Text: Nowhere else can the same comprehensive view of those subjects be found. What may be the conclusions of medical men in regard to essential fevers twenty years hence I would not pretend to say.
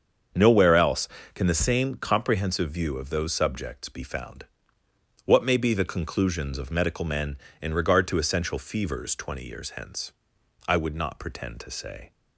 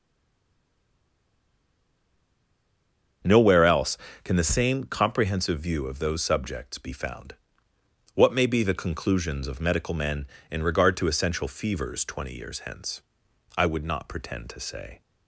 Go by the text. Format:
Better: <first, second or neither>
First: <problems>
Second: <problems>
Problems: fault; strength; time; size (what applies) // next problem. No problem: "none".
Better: first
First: starts louder than the rest; until 1.6 s; 7 dB // pauses between "hence" and "I"; noticeable; at 10.1 s; 0.56 s long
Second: stays silent before the first word; strong; until 3.2 s; 3.2 s long // starts louder than the rest; until 4.5 s; 7 dB // pauses between "hence" and "I"; noticeable; at 13.0 s; 0.56 s long